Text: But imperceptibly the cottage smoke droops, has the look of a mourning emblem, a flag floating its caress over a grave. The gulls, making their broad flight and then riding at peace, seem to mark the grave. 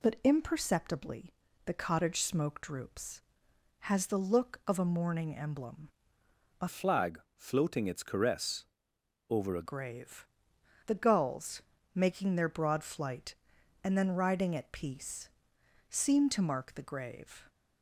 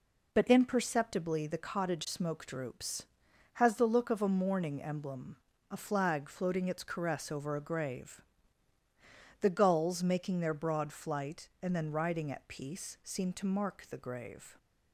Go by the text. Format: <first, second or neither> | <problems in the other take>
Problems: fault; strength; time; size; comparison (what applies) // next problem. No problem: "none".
second | pauses between "imperceptibly" and "the"; slight; at 1.3 s; 0.32 s long // changes voice from "flag" to "a"; from 6.6 to 9.6 s; 3.0 s long // pauses between "flag" and "floating"; slight; at 7.1 s; 0.16 s long // pauses between "caress" and "over"; noticeable; at 8.6 s; 0.64 s long